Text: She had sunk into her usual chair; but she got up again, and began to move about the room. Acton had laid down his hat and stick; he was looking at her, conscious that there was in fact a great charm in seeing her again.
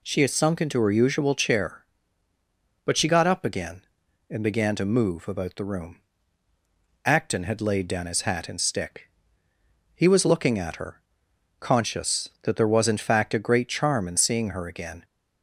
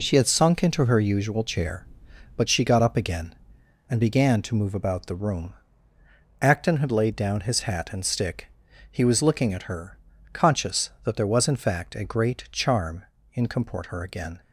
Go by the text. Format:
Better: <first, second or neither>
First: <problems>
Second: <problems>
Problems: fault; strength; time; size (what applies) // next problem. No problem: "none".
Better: first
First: none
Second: says "comport" for "seeing"; at 13.4 s